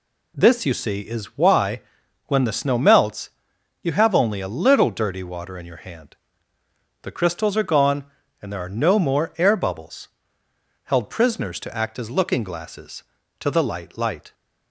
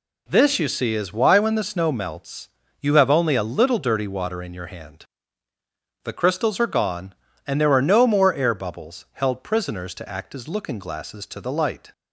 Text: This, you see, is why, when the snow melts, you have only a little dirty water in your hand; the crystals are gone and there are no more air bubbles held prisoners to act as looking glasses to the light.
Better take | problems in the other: second | pauses between "bubbles" and "held"; noticeable; at 10.0 s; 0.74 s long // says "light" twice; at 13.9 s

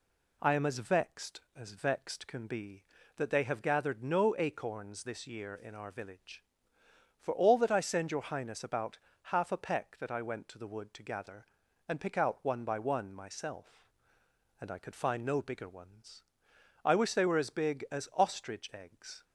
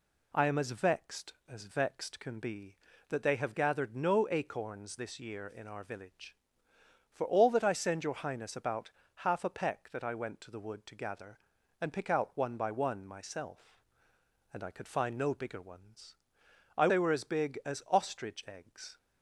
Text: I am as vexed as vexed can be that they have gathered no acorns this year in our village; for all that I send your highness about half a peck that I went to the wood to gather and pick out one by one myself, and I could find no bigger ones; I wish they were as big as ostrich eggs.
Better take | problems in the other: first | pauses between "about" and "half"; slight; at 8.9 s; 0.24 s long; slight in the first // skips "wish"; at 16.8 s

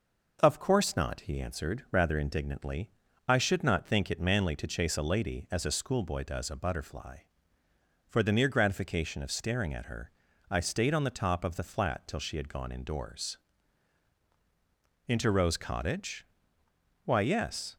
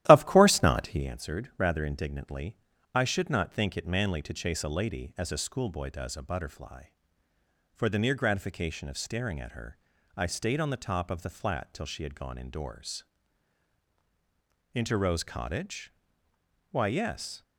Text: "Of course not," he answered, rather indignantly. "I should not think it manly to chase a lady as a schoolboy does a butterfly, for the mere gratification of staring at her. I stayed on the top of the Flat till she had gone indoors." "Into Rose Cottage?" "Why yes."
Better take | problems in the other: first | starts louder than the rest; strong; until 1.1 s; 13.5 dB

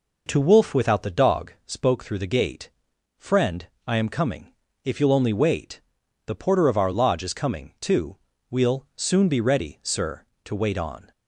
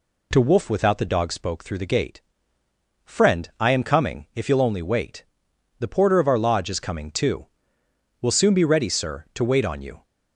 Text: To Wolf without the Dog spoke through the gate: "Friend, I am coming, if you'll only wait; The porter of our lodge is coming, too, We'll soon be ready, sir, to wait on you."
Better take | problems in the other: second | stops before "you"; at 11.1 s

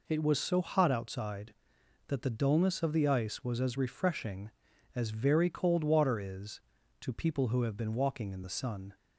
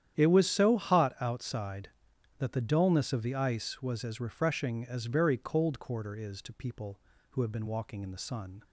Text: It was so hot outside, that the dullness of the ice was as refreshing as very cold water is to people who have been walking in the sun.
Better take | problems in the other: first | starts louder than the rest; strong; until 1.2 s; 10 dB // says "quarter" for "water"; at 5.8 s

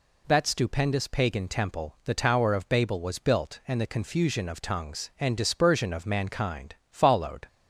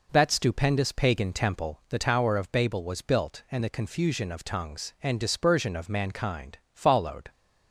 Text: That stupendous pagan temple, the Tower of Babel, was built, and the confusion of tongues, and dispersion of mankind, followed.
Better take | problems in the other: first | starts louder than the rest; noticeable; until 1.8 s; 4.5 dB

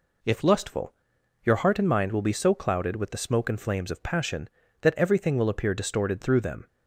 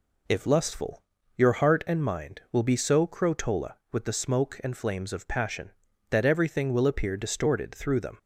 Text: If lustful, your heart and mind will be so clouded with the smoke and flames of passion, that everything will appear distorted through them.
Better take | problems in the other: first | says "crotola" for "clouded"; at 3.0 s

